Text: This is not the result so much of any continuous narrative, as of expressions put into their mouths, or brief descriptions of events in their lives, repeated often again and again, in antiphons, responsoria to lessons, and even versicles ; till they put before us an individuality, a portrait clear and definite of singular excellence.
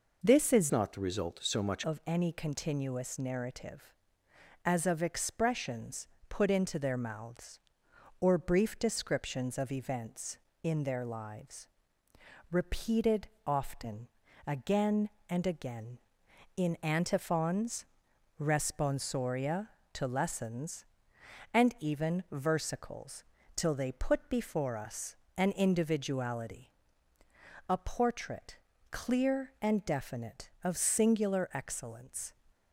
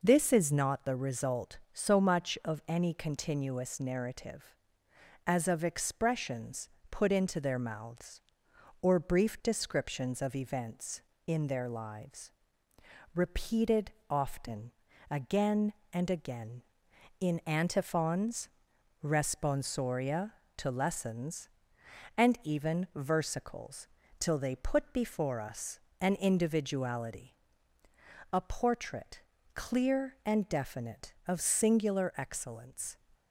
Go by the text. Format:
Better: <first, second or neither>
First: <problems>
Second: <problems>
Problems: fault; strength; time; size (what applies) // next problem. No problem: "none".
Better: second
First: changes voice from "not" to "much"; from 0.7 to 1.8 s; 1.1 s long // pauses between "expressions" and "put"; slight; at 6.0 s; 0.20 s long // pauses between "repeated" and "often"; slight; at 13.2 s; 0.18 s long // pauses between "often" and "again"; at 14.0 s; 0.38 s long // pauses between "us" and "an"; slight; at 25.1 s; 0.22 s long // pauses between "portrait" and "clear"; slight; at 28.5 s; 0.34 s long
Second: pauses between "expressions" and "put"; slight; at 6.6 s; 0.20 s long // pauses between "repeated" and "often"; slight; at 13.9 s; 0.18 s long // pauses between "often" and "again"; at 14.7 s; 0.38 s long // pauses between "us" and "an"; slight; at 25.7 s; 0.22 s long // pauses between "portrait" and "clear"; slight; at 29.2 s; 0.34 s long